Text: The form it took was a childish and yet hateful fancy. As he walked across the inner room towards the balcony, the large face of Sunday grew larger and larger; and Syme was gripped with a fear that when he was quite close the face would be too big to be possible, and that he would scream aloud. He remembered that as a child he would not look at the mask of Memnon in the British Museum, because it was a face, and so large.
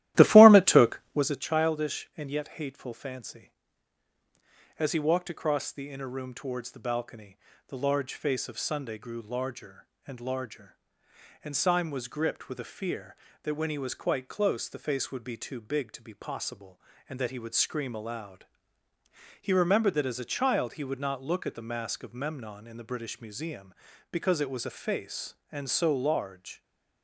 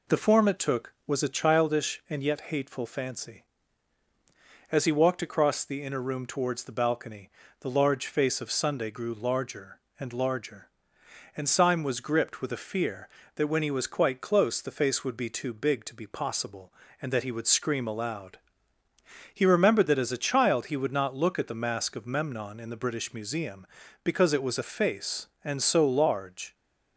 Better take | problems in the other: second | starts louder than the rest; strong; until 1.4 s; 14.5 dB

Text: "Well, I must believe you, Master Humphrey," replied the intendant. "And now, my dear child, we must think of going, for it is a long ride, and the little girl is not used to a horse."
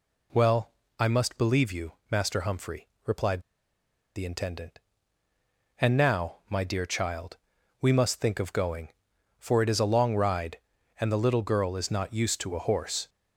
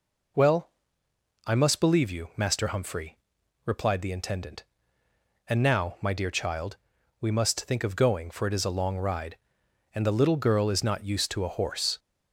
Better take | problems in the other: second | pauses between "replied" and "the"; noticeable; at 3.4 s; 0.74 s long

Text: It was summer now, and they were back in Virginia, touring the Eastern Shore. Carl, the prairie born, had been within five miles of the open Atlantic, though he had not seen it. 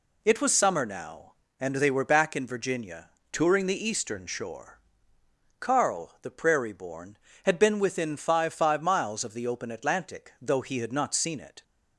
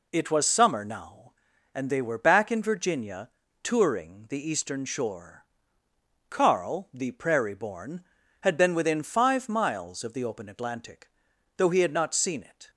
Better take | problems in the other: second | says "five" twice; at 8.5 s

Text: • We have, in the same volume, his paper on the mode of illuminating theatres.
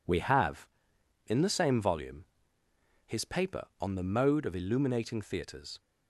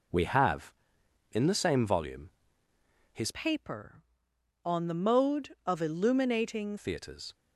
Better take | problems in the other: first | changes voice from "paper" to "illuminating"; from 3.3 to 6.7 s; 3.4 s long

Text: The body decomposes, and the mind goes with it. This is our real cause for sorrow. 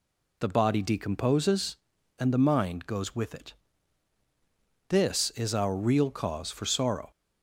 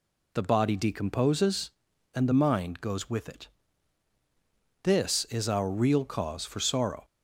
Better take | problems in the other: neither | none

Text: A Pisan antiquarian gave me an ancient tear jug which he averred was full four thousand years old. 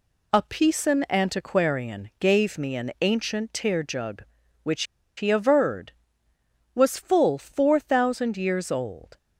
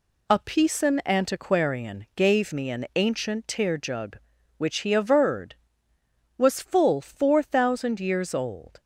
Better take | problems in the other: second | pauses between "which" and "he"; slight; at 4.8 s; 0.33 s long

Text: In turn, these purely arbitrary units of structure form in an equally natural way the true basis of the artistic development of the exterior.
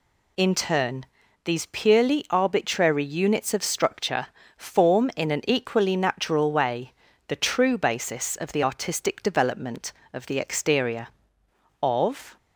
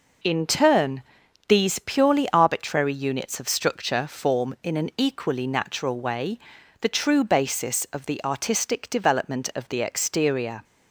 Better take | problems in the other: second | pauses between "structure" and "form"; slight; at 4.2 s; 0.28 s long // pauses between "way" and "the"; slight; at 6.9 s; 0.36 s long; also in the second // goes on to say "Of"; from 11.8 s on; 0.54 s long

